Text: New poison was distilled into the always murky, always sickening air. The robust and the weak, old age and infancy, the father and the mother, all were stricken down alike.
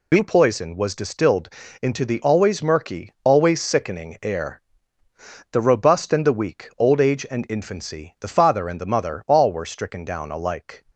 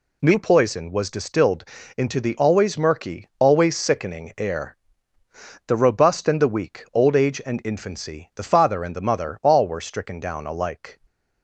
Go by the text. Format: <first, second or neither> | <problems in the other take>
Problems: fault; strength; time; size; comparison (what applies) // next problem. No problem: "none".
second | loses the start of "New"; at 0.1 s; 50 ms // pauses between "distilled" and "into"; slight; at 1.4 s; 0.32 s long; slight in the second